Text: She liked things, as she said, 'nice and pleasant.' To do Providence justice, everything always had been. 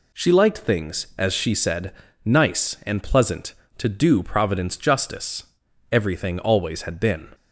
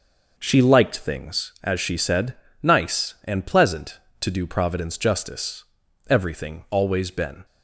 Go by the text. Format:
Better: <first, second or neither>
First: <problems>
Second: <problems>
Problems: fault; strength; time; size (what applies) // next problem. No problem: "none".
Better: first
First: none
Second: skips "had"; at 7.1 s